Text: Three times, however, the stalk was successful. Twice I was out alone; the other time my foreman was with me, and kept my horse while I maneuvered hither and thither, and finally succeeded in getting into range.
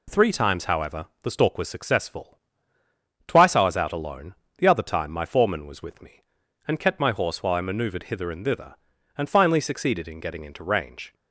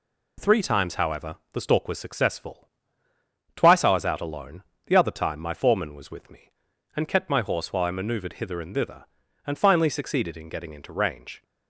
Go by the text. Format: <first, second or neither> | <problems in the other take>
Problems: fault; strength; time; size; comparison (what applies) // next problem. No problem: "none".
neither | none